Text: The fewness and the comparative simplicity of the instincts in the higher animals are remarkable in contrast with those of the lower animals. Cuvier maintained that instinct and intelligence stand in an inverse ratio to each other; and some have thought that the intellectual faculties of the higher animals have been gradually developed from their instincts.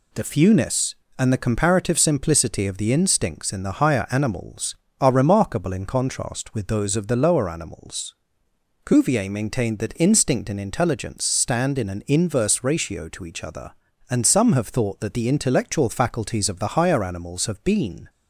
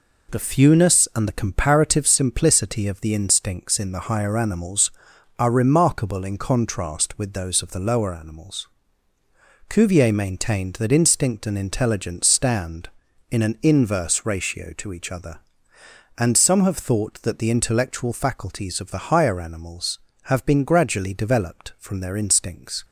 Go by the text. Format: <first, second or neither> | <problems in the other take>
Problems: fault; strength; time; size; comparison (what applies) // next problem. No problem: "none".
second | stops before "gradually developed from their instincts"; at 18.0 s